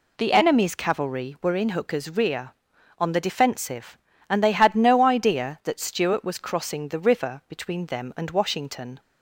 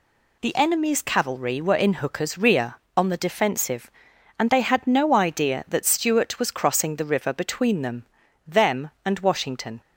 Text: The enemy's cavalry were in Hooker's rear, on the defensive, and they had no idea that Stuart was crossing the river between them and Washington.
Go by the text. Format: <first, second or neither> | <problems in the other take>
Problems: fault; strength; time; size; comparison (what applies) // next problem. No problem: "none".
first | says "them" twice; at 8.4 s